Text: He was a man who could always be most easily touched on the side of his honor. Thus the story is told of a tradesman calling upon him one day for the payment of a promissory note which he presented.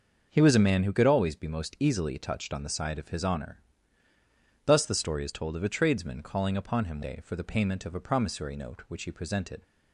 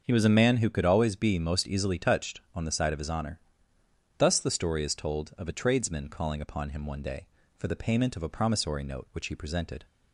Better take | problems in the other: second | starts louder than the rest; until 1.3 s; 6.5 dB; also in the second // skips "one"; at 7.0 s

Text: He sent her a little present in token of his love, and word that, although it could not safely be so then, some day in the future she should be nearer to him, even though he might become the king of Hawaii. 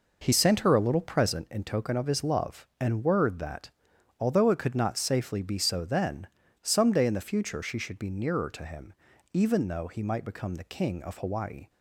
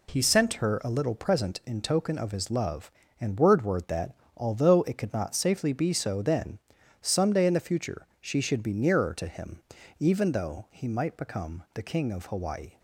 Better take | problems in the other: first | says "word" twice; at 3.6 s

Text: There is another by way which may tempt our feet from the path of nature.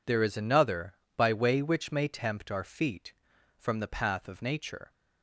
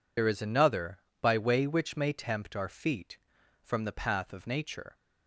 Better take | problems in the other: first | loses the start of "There"; at 0.1 s; 70 ms

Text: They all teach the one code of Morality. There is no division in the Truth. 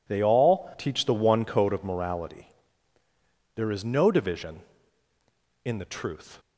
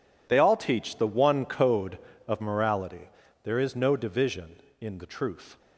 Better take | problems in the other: neither | none

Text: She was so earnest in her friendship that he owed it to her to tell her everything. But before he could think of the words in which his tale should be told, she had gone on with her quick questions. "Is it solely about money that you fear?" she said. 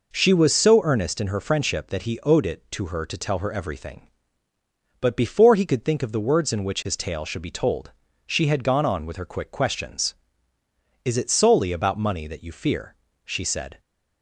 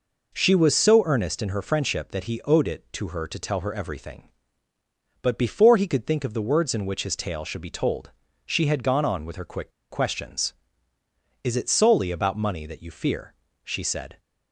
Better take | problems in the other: first | pauses between "quick" and "questions"; slight; at 9.6 s; 0.21 s long

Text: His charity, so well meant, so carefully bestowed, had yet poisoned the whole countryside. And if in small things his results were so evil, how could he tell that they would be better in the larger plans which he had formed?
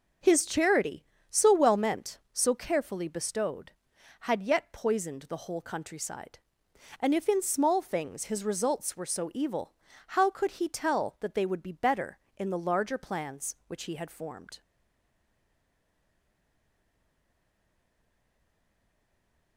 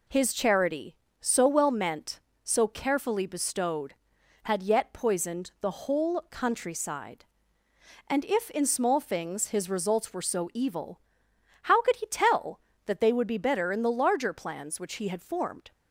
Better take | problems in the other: second | starts louder than the rest; noticeable; until 1.4 s; 6 dB // stays silent after the last word; strong; from 14.6 s on; 4.9 s long

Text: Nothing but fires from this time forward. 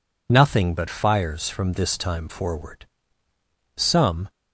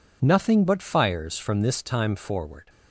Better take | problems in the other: second | goes on to say "Some"; from 3.7 s on; 0.54 s long

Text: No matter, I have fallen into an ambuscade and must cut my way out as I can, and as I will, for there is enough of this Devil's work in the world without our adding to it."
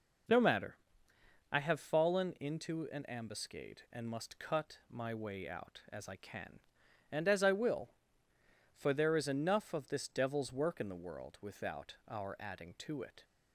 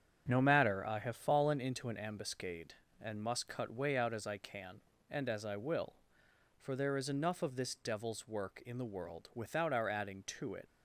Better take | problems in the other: first | starts louder than the rest; strong; until 1.2 s; 8 dB // skips "my"; at 3.7 s

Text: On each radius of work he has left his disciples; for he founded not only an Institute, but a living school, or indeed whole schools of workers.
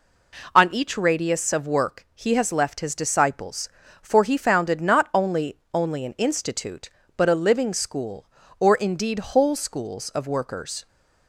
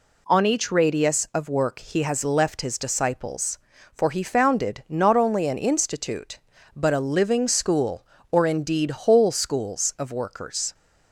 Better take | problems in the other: second | says "only" twice; at 5.7 s

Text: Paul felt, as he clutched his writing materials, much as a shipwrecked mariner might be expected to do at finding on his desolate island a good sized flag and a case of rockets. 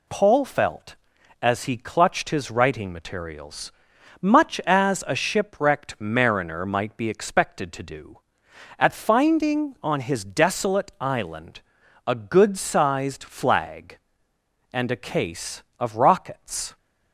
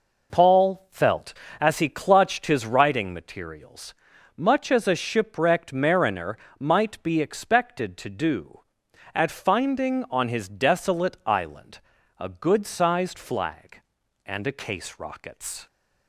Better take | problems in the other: first | pauses between "mariner" and "might"; slight; at 6.3 s; 0.22 s long // pauses between "island" and "a"; at 11.8 s; 0.38 s long; noticeable in the first // skips "of"; at 14.9 s

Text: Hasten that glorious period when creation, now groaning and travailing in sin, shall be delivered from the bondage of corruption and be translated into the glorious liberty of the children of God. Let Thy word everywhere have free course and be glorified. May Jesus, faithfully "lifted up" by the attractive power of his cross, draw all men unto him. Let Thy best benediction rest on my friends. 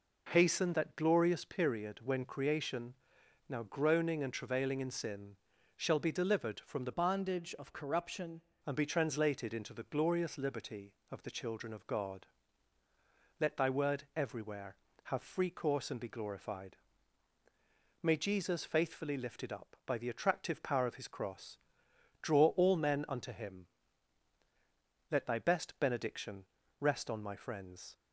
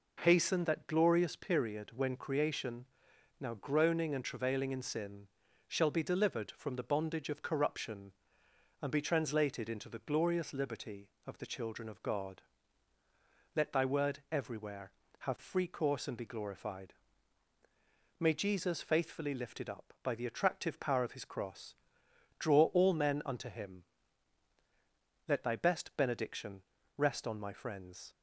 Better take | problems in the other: second | changes voice from "bondage" to "corruption"; from 6.9 to 8.4 s; 1.5 s long // pauses between "benediction" and "rest"; at 26.4 s; 0.38 s long; also in the second

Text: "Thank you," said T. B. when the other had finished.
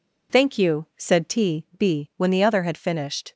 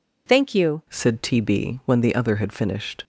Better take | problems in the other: first | changes voice at "said"; from 0.8 s on; 2.2 s long

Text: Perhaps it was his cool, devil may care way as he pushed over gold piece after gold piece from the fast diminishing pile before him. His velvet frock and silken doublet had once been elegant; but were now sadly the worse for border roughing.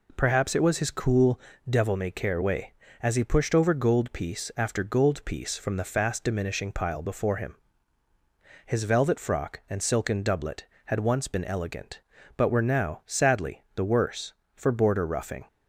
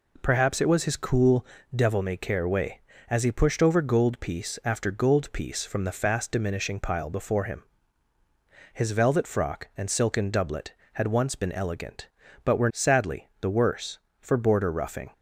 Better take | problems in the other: first | skips "now"; at 12.7 s

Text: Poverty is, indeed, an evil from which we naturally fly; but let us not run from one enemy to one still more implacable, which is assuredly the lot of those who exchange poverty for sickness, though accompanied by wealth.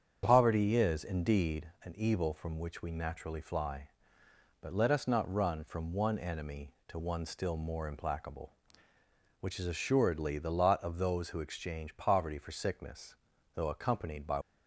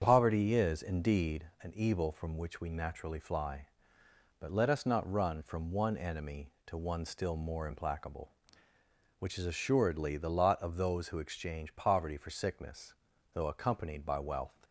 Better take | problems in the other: second | starts louder than the rest; strong; until 1.2 s; 7.5 dB; strong in the second // stops before "wealth"; at 14.4 s

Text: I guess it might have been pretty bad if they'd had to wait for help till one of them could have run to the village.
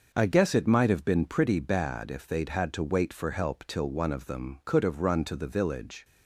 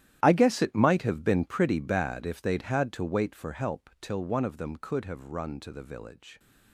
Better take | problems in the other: first | gets quieter; strong; throughout; 16.5 dB // starts louder than the rest; strong; until 1.2 s; 12 dB; noticeable in the first

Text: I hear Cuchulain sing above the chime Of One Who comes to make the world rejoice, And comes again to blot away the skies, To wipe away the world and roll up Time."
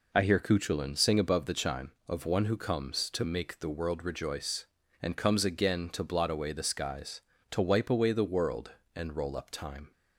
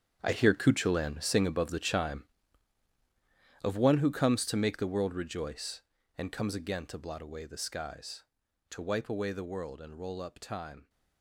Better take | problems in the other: first | gets quieter; strong; throughout; 14 dB

